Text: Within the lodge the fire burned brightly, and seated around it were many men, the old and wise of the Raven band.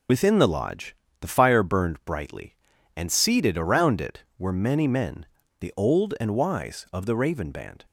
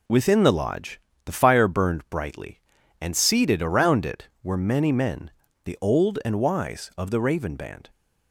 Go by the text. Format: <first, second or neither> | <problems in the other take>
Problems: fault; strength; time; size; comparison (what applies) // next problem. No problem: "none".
second | loses the start of "Within"; at 0.0 s; 65 ms // pauses between "lodge" and "the"; slight; at 0.9 s; 0.26 s long; slight in the second